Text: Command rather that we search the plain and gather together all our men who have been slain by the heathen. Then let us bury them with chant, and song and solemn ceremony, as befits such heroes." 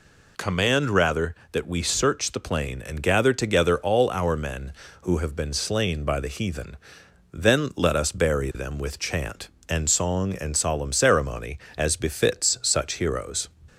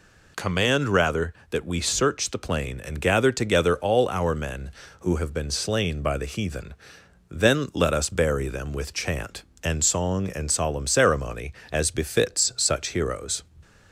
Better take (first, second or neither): neither